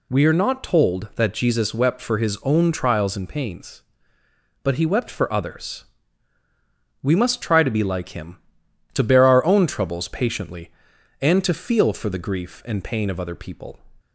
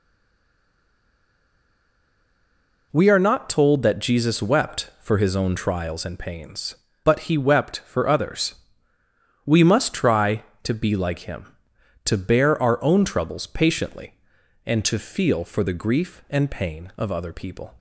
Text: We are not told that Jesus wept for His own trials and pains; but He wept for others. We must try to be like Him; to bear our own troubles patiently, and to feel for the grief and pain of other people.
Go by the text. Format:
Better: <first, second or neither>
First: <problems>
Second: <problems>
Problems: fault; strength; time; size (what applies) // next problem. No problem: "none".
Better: first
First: none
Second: stays silent before the first word; strong; until 2.9 s; 2.9 s long